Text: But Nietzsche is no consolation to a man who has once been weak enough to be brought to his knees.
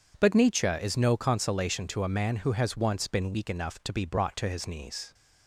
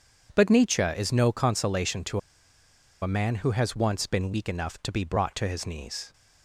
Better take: first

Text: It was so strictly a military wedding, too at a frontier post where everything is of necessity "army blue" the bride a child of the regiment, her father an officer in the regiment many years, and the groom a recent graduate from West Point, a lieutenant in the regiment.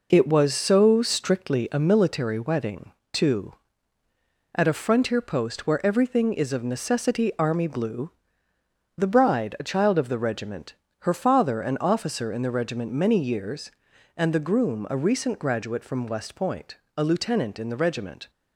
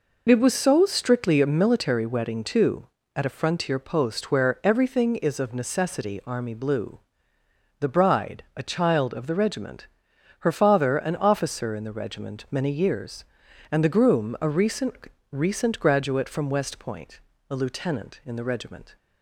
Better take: first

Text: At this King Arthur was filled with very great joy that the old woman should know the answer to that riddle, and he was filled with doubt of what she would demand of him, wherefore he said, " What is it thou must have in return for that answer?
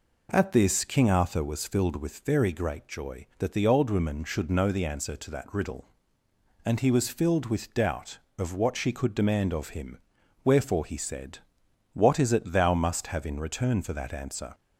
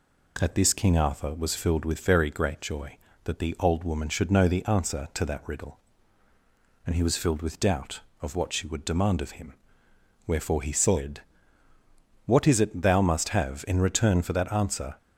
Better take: second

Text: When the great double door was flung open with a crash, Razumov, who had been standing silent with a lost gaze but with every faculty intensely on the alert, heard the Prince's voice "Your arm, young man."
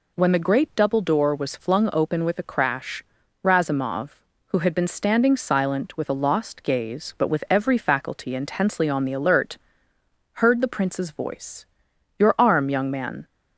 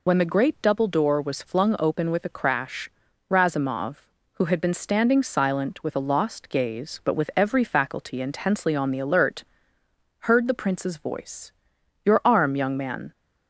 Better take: first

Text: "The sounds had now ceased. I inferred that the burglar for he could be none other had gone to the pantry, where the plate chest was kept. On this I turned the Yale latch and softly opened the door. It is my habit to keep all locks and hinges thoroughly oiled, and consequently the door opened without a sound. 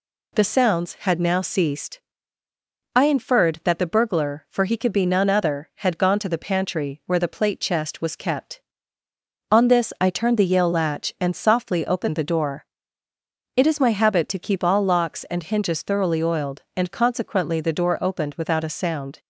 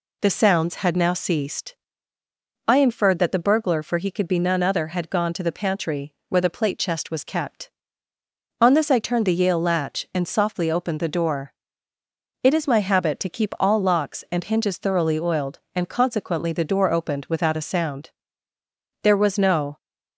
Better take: first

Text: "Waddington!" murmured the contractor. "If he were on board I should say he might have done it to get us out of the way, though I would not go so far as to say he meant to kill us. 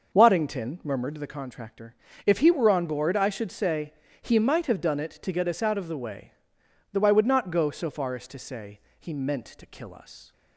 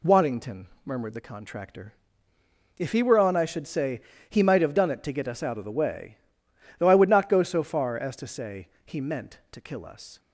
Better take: first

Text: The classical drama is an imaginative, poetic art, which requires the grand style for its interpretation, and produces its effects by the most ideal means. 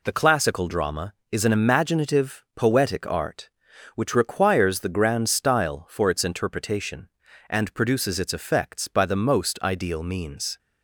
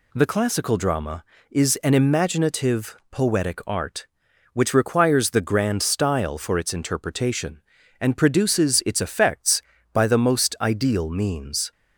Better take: neither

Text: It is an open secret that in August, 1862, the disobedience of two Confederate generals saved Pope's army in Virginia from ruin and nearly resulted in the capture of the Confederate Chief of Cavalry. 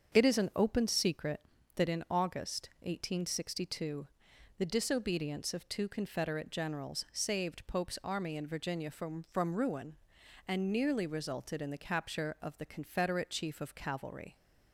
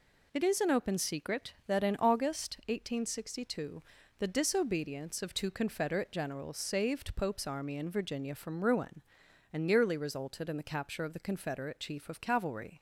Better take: second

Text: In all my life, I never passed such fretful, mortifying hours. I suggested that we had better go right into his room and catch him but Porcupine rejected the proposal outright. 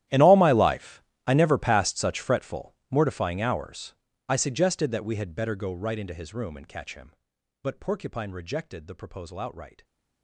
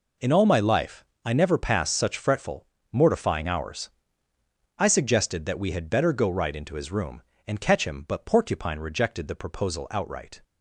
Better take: second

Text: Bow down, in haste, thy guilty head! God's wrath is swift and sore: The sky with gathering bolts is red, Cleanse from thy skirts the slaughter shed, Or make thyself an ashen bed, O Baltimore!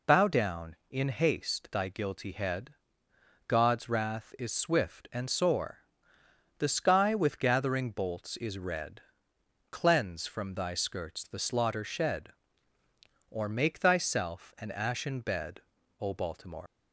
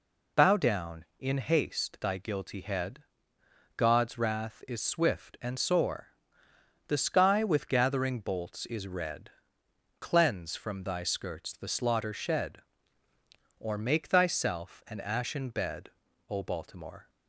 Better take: second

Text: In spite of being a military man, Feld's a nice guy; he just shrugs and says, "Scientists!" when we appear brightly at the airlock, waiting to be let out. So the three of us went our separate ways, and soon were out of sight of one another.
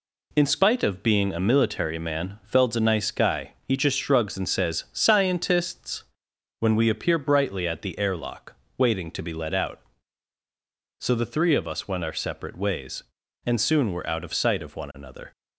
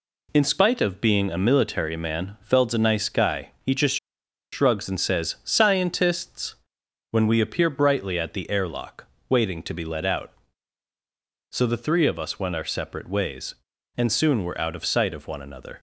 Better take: first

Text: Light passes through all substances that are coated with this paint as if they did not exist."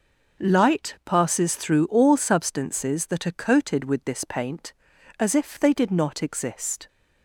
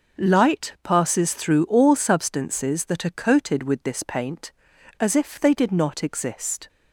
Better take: neither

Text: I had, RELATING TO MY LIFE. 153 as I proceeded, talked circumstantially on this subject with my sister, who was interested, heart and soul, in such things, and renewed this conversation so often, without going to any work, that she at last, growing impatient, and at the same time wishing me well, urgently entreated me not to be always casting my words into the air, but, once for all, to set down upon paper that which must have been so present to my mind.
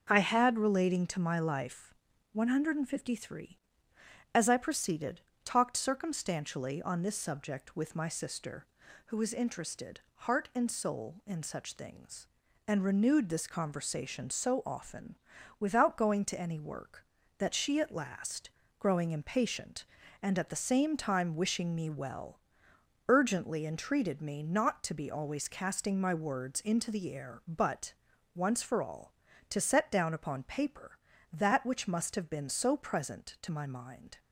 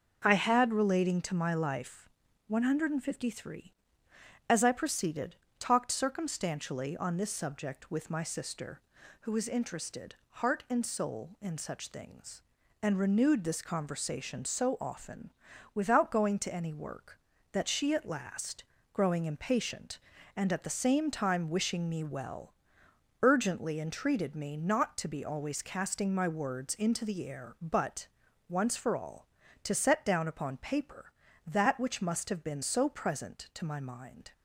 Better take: neither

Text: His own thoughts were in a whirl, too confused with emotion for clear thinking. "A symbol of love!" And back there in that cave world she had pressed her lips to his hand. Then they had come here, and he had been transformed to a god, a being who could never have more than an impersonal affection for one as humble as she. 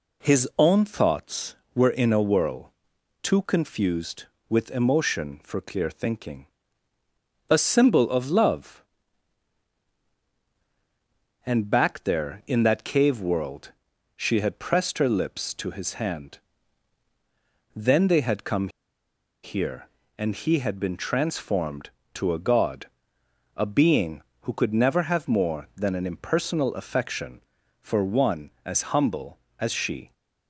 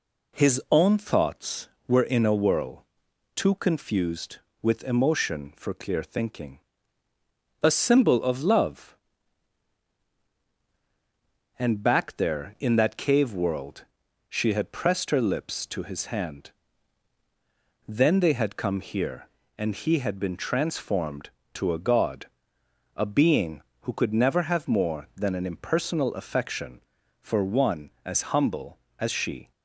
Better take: second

